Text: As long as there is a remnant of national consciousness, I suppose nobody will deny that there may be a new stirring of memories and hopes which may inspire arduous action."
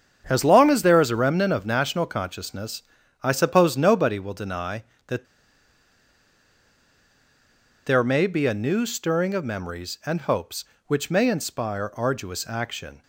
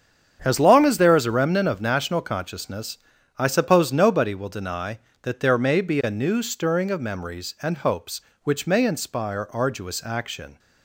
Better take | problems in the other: second | starts louder than the rest; strong; until 1.2 s; 8 dB; strong in the second // pauses between "that" and "there"; strong; at 5.2 s; 2.6 s long

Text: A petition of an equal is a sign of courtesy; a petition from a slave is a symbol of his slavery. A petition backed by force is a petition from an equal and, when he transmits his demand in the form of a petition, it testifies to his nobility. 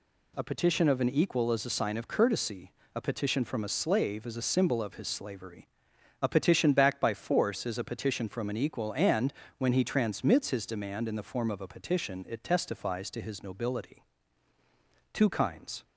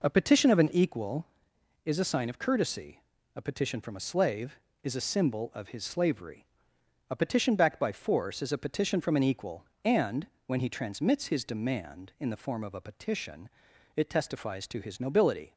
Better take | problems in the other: second | goes on to say "Two kinds"; noticeable; from 15.1 s on; 0.70 s long

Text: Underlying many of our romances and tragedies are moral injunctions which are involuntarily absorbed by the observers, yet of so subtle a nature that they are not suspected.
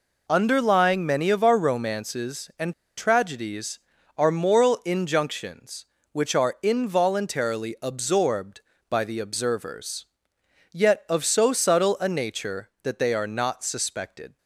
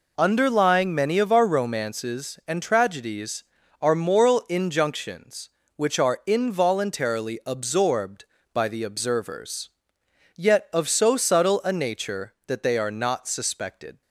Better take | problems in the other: second | pauses between "and" and "tragedies"; slight; at 2.7 s; 0.23 s long

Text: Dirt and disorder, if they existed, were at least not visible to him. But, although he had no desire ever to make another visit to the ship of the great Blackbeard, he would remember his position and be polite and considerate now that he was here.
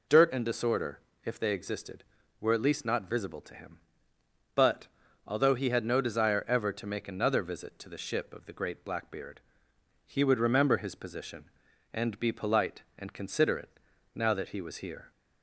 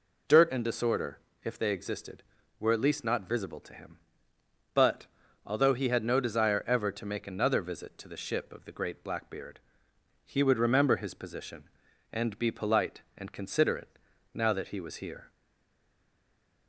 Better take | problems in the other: first | pauses between "considerate" and "now"; slight; at 13.9 s; 0.36 s long; slight in the first // stays silent after the last word; noticeable; from 15.3 s on; 1.3 s long

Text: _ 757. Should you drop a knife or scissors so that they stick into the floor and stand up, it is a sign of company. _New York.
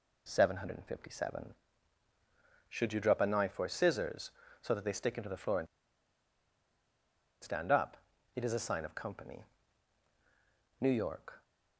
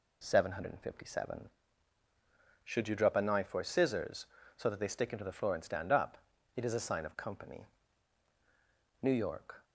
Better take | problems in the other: second | pauses between "and" and "stand"; strong; at 5.6 s; 1.7 s long

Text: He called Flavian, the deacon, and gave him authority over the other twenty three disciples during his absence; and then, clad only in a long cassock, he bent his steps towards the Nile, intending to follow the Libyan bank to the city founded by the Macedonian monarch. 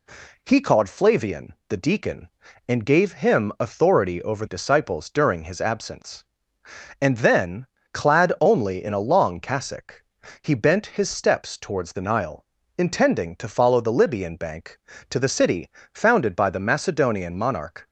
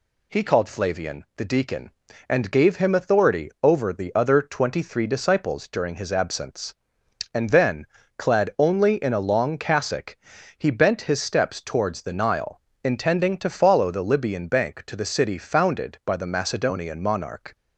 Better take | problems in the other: second | skips "the other twenty three"; at 4.4 s // pauses between "city" and "founded"; slight; at 15.6 s; 0.24 s long

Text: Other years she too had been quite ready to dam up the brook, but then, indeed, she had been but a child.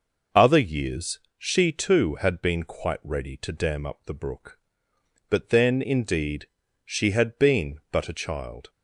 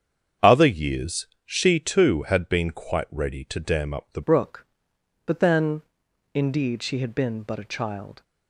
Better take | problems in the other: first | starts louder than the rest; strong; until 1.5 s; 7.5 dB // pauses between "years" and "she"; slight; at 1.2 s; 0.18 s long; slight in the first // changes voice at "brook"; from 4.2 s on; 4.0 s long

